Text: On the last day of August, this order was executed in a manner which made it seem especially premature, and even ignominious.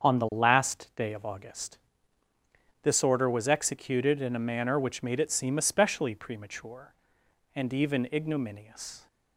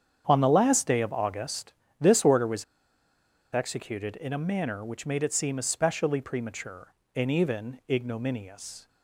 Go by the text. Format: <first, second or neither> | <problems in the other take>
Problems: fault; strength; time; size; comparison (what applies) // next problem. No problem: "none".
first | starts louder than the rest; strong; until 1.2 s; 8.5 dB; strong in the first // pauses between "was" and "executed"; noticeable; at 2.6 s; 0.89 s long